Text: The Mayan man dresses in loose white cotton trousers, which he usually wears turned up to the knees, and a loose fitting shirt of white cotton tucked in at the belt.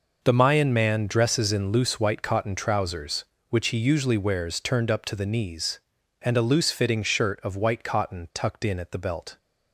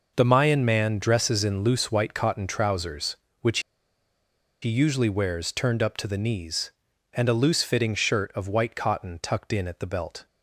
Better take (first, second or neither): first